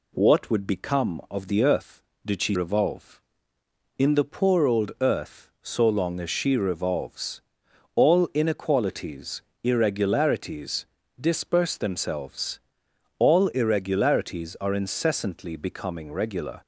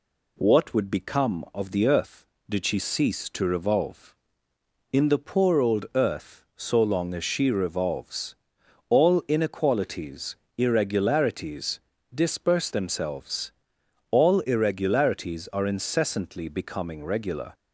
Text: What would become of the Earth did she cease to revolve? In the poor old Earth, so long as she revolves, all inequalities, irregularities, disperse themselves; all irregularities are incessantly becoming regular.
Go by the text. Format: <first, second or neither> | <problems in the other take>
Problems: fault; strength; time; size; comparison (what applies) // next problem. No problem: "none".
second | skips "cease to"; at 2.5 s